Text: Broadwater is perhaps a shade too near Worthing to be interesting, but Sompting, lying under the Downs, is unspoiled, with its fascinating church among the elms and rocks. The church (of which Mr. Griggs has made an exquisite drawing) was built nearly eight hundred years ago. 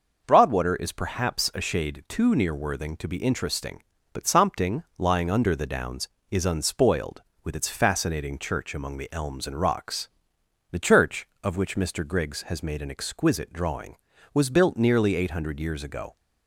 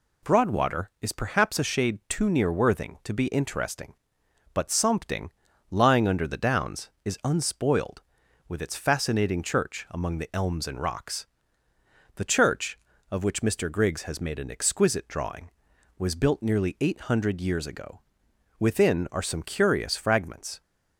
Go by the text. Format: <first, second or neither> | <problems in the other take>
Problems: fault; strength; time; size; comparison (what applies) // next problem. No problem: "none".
first | goes on to say "Within are some curious fragments"; strong; from 18.5 s on; 2.0 s long